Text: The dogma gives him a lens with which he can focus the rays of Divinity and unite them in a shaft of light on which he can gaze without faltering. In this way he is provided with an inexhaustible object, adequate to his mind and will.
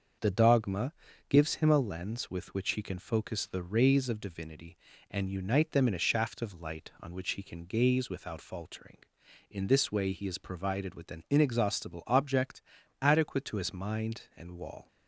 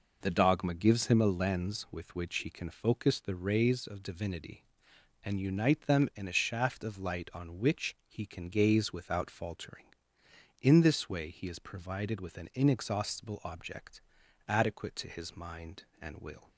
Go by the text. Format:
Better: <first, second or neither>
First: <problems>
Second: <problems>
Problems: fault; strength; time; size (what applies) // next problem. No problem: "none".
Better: second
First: starts louder than the rest; until 1.5 s; 6.5 dB // pauses between "dogma" and "gives"; slight; at 0.9 s; 0.36 s long // says "wall" for "will"; at 14.5 s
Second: none